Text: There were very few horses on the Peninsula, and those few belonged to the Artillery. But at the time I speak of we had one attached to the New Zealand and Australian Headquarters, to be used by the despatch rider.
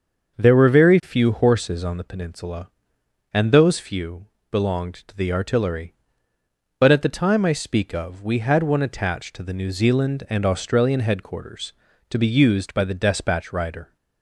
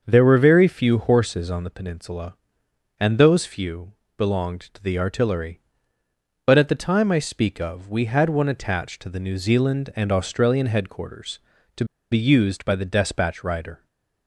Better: first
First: starts louder than the rest; until 1.4 s; 6.5 dB // pauses between "few" and "belonged"; slight; at 4.2 s; 0.24 s long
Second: starts louder than the rest; until 1.0 s; 6.5 dB // pauses between "few" and "belonged"; slight; at 3.9 s; 0.24 s long // pauses between "to" and "be"; slight; at 11.8 s; 0.27 s long // stays silent after the last word; slight; from 13.7 s on; 0.5 s long

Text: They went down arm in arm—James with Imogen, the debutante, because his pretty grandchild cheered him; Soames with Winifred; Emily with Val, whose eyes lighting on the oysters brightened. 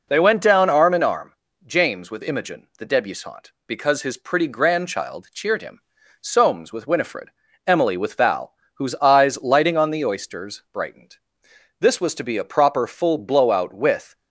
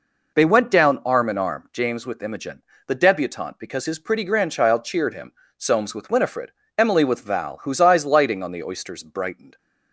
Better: second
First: goes on to say "This was to be a proper full blowout with"; strong; from 11.7 s on; 2.3 s long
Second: none

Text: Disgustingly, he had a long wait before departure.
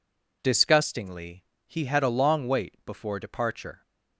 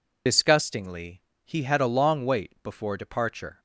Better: first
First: none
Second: loses the start of "Disgustingly"; at 0.2 s; 65 ms

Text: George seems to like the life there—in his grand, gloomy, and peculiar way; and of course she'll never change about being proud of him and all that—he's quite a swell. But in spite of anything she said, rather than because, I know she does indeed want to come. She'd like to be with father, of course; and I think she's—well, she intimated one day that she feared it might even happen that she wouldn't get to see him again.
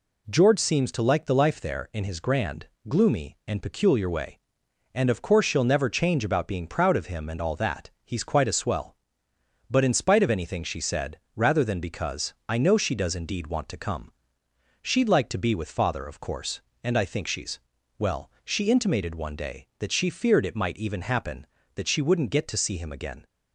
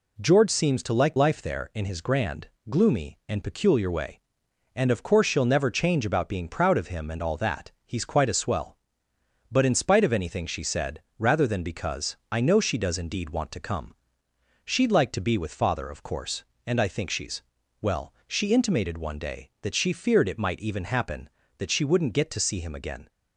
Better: first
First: none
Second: skips "the"; at 1.1 s

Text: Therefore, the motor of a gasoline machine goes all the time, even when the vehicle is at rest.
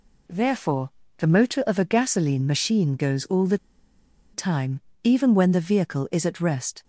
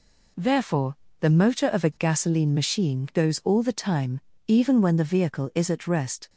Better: second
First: pauses between "the" and "time"; noticeable; at 3.5 s; 0.75 s long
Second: none

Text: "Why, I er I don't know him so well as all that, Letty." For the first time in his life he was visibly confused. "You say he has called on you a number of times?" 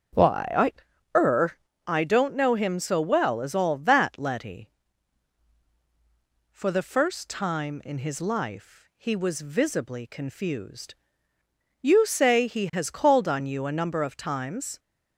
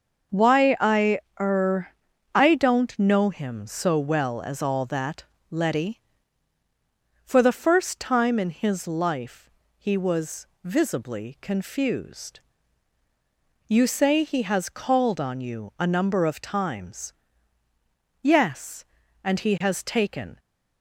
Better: first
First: starts louder than the rest; strong; until 1.9 s; 7.5 dB // pauses between "er" and "I"; slight; at 1.5 s; 0.30 s long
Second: starts louder than the rest; until 1.5 s; 6 dB // pauses between "I" and "er"; slight; at 1.1 s; 0.22 s long // pauses between "er" and "I"; at 1.8 s; 0.44 s long // pauses between "life" and "he"; slight; at 9.4 s; 0.28 s long // pauses between "was" and "visibly"; slight; at 10.4 s; 0.16 s long // goes on to say "Yes and he has taken"; strong; from 18.2 s on; 2.1 s long

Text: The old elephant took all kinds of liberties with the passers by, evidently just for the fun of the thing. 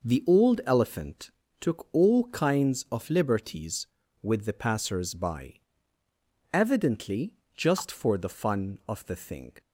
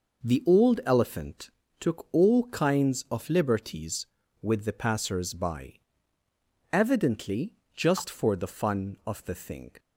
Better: neither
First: pauses between "elephant" and "took"; slight; at 1.2 s; 0.30 s long // pauses between "evidently" and "just"; slight; at 7.3 s; 0.22 s long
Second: pauses between "elephant" and "took"; slight; at 1.4 s; 0.30 s long // pauses between "evidently" and "just"; slight; at 7.5 s; 0.22 s long

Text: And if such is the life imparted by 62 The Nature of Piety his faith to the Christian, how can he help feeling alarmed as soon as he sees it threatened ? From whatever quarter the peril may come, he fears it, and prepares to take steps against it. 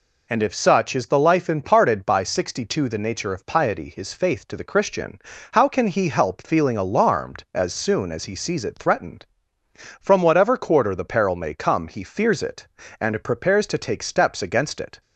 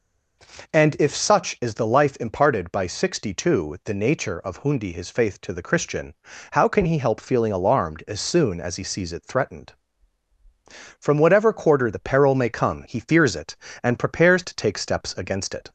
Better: first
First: none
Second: says "Hundi" for "Piety"; at 4.6 s

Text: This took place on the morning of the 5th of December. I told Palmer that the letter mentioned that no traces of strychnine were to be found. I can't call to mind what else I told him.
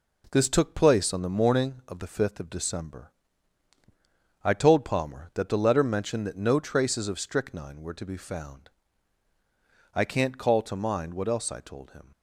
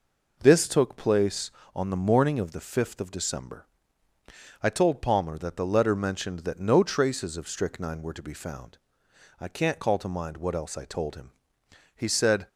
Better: first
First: none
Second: goes on to say "He said"; from 11.9 s on; 0.52 s long

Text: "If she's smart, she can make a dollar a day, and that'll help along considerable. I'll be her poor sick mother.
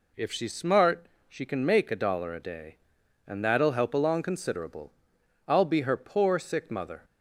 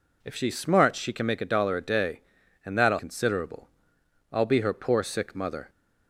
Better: first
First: none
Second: skips "help along"; at 2.9 s

